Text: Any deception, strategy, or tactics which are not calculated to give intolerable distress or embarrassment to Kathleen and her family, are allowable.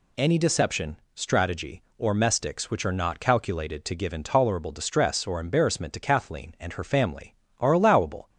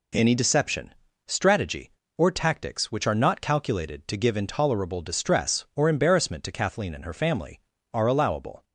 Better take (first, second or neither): second